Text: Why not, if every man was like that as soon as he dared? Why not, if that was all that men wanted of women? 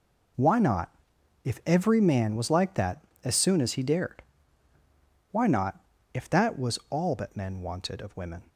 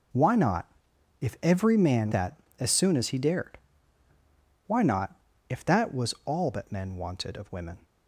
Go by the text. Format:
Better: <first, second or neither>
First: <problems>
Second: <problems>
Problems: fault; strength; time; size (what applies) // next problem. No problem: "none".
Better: first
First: none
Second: skips "was like"; at 2.1 s